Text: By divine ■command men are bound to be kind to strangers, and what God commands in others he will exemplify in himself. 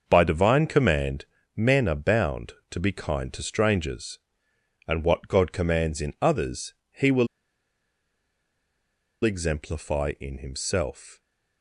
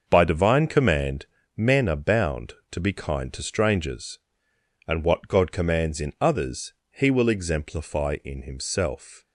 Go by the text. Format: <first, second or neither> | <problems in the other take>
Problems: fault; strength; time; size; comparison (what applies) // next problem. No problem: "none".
second | starts louder than the rest; until 1.0 s; 6.5 dB; also in the second // pauses between "command" and "men"; slight; at 1.2 s; 0.30 s long; slight in the second // pauses between "others" and "he"; slight; at 6.7 s; 0.18 s long; slight in the second // pauses between "will" and "exemplify"; strong; at 7.2 s; 1.9 s long